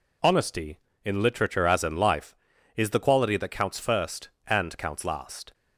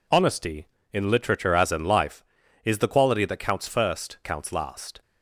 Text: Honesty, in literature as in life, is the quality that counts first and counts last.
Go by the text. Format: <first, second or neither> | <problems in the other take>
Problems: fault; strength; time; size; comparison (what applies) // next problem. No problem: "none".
first | skips "and"; at 4.1 s